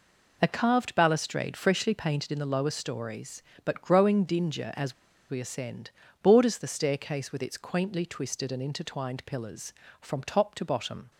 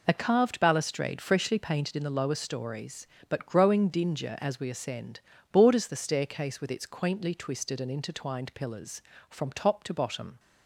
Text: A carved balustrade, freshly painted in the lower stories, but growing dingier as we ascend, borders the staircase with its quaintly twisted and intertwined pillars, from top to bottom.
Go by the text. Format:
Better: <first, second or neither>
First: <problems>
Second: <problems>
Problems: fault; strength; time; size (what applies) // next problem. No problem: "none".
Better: second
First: pauses between "as" and "we"; at 4.9 s; 0.36 s long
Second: none